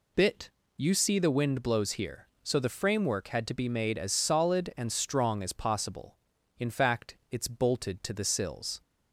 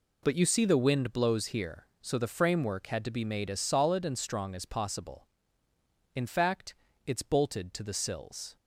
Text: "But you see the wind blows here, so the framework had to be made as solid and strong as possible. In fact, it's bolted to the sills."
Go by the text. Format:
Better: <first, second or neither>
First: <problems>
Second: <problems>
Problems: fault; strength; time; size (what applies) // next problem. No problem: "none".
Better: second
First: says "Bit" for "But"; at 0.1 s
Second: none